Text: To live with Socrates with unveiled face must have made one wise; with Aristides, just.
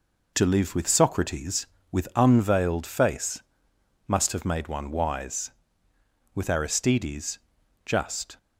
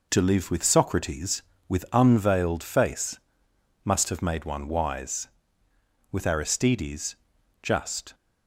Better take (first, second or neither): neither